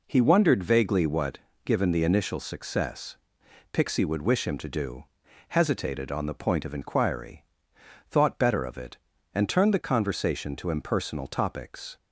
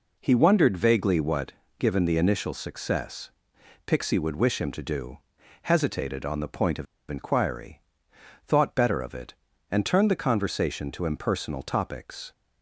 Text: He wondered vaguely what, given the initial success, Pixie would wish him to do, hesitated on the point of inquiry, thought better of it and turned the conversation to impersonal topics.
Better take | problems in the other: first | pauses between "of" and "inquiry"; slight; at 6.8 s; 0.24 s long

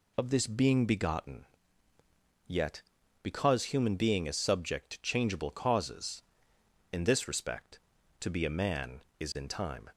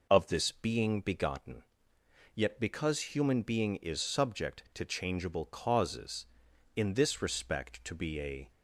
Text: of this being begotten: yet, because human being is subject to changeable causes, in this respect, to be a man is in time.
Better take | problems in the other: first | stops before "man is in time"; at 8.5 s

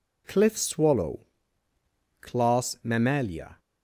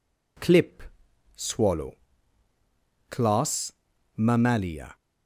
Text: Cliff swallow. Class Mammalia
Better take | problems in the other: first | says "Clip" for "Cliff"; at 0.3 s // pauses between "Class" and "Mammalia"; at 3.7 s; 0.44 s long

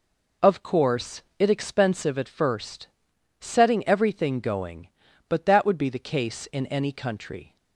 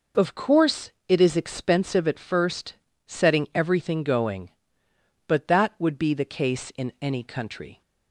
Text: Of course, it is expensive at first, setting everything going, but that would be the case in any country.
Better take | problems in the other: second | skips "is"; at 1.4 s

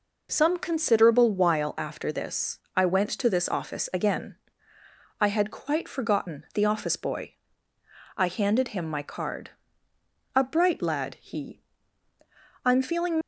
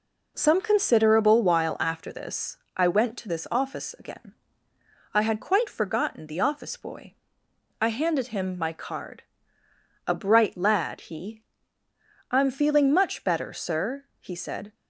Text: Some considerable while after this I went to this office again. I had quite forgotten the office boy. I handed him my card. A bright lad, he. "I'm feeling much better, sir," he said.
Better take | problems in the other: second | pauses between "this" and "I"; slight; at 2.6 s; 0.16 s long; slight in the second // stops before "much better sir he said"; at 13.2 s

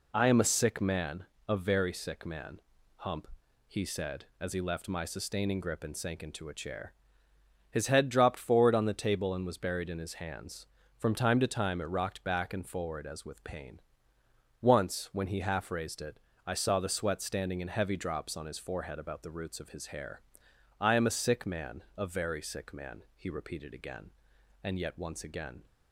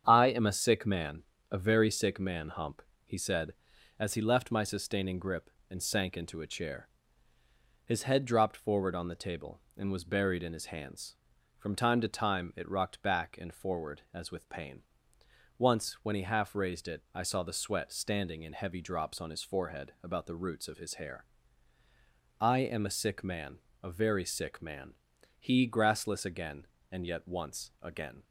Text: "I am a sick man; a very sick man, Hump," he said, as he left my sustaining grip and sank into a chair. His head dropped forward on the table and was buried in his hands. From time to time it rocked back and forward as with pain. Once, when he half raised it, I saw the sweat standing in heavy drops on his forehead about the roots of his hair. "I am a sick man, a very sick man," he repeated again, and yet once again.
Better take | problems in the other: first | starts louder than the rest; strong; until 1.0 s; 8.5 dB // says "grassless" for "repeated"; at 25.6 s

